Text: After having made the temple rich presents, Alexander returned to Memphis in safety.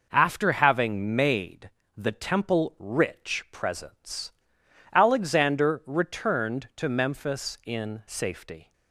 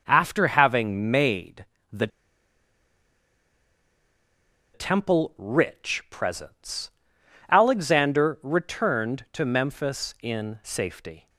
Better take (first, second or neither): first